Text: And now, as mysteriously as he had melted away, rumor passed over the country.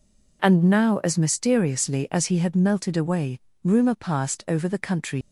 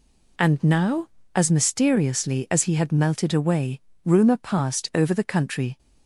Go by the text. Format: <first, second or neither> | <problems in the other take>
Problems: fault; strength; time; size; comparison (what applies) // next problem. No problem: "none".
second | leaves "country" unfinished; at 5.2 s; 115 ms